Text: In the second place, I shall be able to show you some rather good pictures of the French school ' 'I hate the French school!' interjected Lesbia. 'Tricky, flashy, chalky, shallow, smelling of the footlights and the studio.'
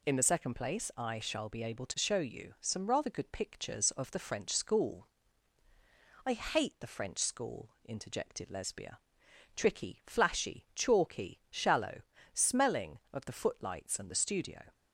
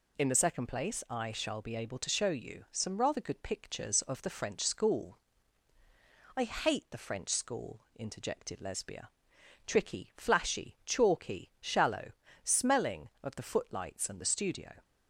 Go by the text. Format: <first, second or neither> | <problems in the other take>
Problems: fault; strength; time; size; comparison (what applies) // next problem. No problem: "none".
neither | none